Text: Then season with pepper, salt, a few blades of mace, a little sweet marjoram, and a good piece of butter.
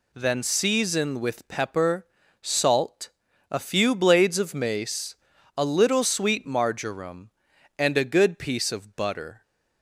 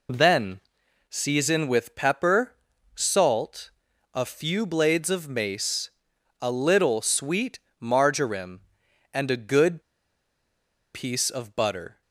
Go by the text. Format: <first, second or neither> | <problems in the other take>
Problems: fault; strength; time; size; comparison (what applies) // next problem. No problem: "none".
first | pauses between "Then" and "season"; noticeable; at 0.6 s; 0.48 s long // pauses between "sweet" and "marjoram"; slight; at 7.5 s; 0.20 s long // pauses between "good" and "piece"; at 9.8 s; 1.1 s long